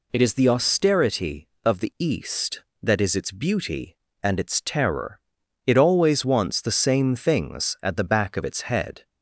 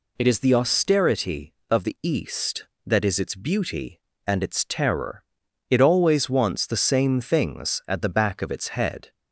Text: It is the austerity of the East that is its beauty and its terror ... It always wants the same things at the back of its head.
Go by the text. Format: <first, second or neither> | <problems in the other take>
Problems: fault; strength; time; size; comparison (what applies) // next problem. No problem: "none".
neither | none